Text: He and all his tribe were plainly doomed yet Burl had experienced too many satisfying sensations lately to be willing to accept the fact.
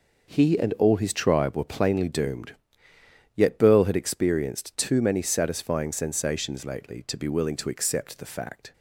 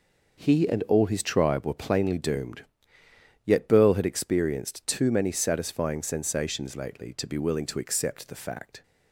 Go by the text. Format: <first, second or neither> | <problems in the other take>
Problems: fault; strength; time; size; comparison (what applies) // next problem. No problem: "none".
neither | pauses between "doomed" and "yet"; noticeable; the same in both